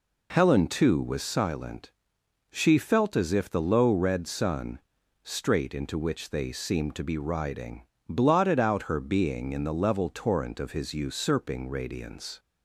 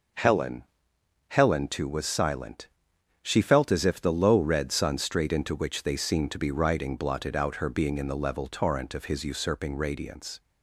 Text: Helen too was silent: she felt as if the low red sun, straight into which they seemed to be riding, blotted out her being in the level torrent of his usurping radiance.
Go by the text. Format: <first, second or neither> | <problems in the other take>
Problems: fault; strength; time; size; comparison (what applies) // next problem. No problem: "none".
first | says "Helen" twice; at 1.2 s